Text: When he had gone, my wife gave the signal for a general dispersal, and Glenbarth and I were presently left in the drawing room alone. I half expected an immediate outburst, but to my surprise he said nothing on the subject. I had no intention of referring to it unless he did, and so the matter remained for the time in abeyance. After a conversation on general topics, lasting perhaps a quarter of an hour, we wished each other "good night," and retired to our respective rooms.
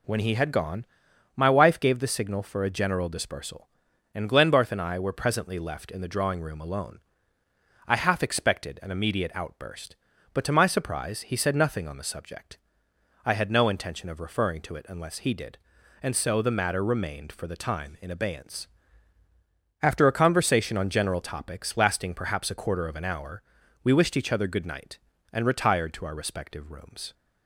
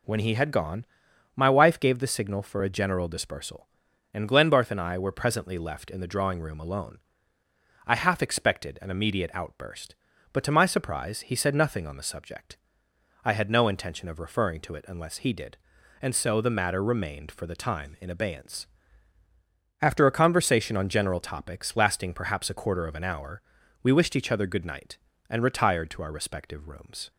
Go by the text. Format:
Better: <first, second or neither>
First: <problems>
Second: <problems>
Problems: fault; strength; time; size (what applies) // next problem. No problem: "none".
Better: neither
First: none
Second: none